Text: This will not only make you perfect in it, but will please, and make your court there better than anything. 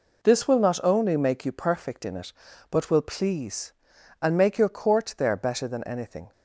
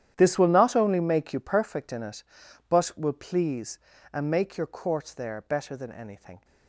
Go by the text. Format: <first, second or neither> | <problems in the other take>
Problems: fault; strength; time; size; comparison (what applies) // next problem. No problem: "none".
first | gets quieter; strong; throughout; 17 dB